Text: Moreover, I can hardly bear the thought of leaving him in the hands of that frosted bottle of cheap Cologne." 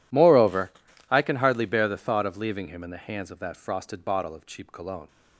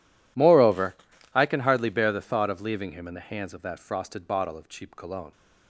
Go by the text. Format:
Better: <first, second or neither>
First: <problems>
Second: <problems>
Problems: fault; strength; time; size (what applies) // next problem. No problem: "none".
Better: neither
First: none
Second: none